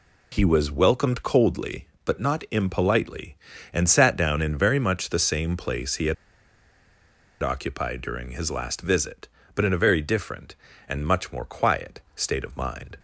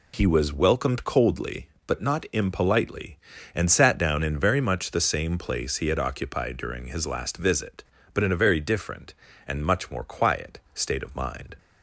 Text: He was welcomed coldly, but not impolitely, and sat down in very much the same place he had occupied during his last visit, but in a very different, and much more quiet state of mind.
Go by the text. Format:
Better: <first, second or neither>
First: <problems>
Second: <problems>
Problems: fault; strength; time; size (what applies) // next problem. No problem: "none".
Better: second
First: pauses between "had" and "occupied"; strong; at 6.1 s; 1.2 s long // pauses between "quiet" and "state"; slight; at 11.9 s; 0.16 s long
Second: pauses between "quiet" and "state"; slight; at 10.5 s; 0.16 s long